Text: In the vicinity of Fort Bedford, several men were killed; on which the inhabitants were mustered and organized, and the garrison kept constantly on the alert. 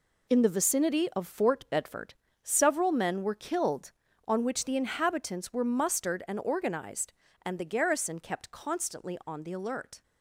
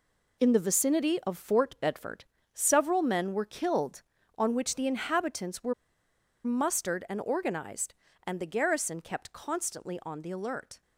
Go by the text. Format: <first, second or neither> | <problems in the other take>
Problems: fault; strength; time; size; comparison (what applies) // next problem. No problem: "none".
first | pauses between "were" and "mustered"; noticeable; at 5.7 s; 0.71 s long